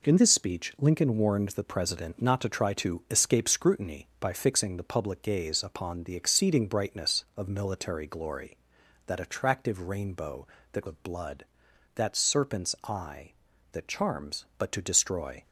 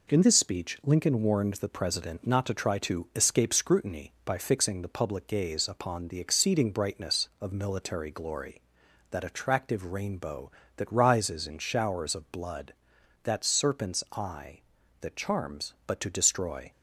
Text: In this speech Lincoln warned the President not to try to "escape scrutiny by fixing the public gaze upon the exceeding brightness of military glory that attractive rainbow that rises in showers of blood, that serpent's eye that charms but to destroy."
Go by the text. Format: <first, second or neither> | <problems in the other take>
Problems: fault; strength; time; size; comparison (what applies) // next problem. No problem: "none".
second | skips "rises in showers"; at 10.8 s